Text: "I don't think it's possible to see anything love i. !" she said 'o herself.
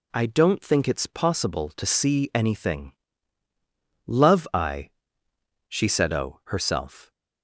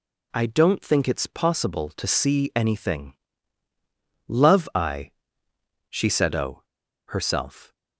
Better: first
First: pauses between "anything" and "love"; at 2.9 s; 1.1 s long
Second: pauses between "anything" and "love"; at 3.1 s; 1.1 s long // pauses between "o" and "herself"; at 6.6 s; 0.44 s long

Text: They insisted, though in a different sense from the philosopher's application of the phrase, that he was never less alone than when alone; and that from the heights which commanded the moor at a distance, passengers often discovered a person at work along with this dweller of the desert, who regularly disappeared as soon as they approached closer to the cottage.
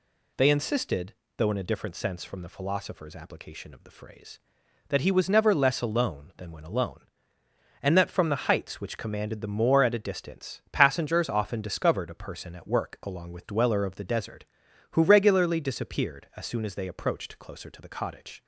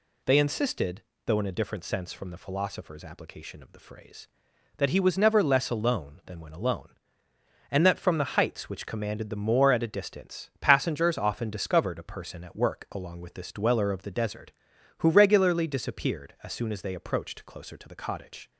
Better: second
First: skips "this"; at 13.4 s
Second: none

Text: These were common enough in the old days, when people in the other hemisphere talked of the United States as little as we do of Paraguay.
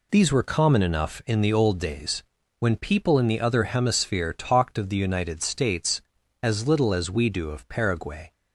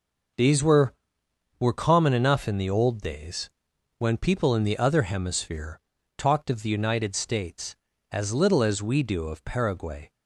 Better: first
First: none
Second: says "were" twice; at 1.5 s // pauses between "hemisphere" and "talked"; at 5.7 s; 0.38 s long

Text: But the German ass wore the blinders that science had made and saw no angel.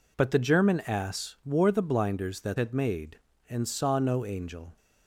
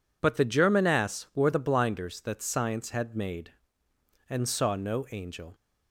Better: second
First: skips "science"; at 2.5 s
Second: none

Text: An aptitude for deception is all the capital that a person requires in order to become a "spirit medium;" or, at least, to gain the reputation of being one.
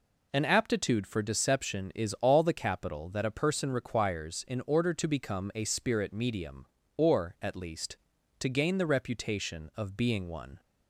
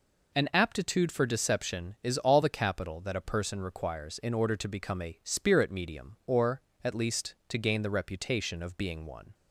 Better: neither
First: none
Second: none

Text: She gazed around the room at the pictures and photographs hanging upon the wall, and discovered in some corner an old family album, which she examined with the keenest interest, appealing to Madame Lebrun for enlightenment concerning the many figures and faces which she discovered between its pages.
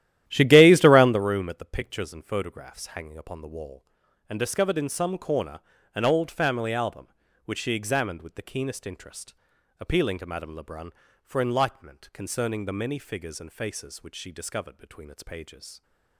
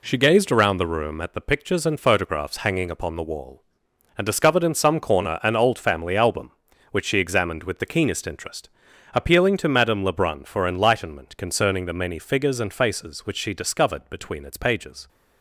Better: second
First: starts louder than the rest; strong; until 1.2 s; 13 dB // pauses between "corner" and "an"; slight; at 5.5 s; 0.34 s long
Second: none

